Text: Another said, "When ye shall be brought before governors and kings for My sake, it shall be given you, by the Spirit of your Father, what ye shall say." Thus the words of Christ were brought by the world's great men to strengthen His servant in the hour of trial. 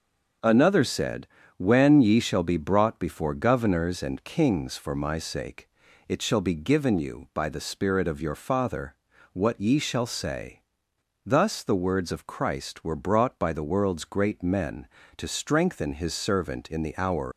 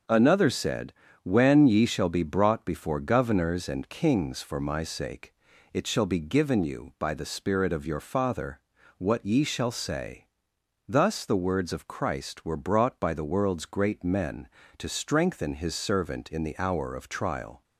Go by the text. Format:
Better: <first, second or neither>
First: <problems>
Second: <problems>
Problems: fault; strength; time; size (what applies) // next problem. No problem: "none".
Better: second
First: stops before "of trial"; at 17.3 s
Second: none